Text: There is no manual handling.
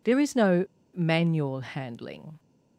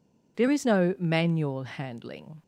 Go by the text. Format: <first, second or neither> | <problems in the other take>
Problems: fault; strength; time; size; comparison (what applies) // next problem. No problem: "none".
second | pauses between "no" and "manual"; slight; at 0.6 s; 0.30 s long